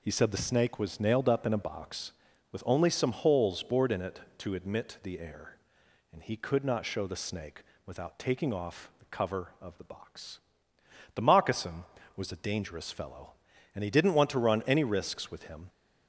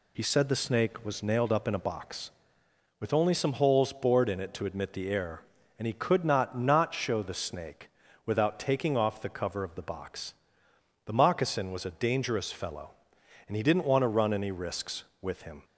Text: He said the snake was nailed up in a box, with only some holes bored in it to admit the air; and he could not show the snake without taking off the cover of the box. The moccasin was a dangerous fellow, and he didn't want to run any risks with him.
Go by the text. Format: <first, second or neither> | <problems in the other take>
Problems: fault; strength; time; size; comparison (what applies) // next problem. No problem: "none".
first | says "not" twice; at 6.5 s // pauses between "snake" and "without"; slight; at 7.9 s; 0.34 s long; slight in the first